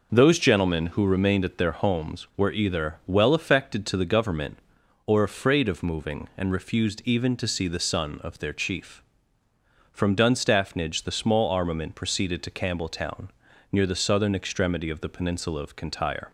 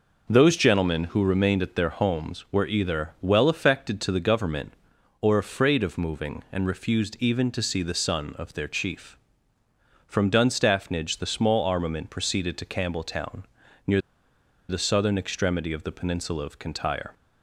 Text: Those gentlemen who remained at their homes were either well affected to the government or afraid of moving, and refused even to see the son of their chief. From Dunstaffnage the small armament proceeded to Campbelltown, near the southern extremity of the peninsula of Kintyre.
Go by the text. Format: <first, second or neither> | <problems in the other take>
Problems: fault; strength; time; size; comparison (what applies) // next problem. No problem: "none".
first | pauses between "near" and "the"; noticeable; at 14.0 s; 0.68 s long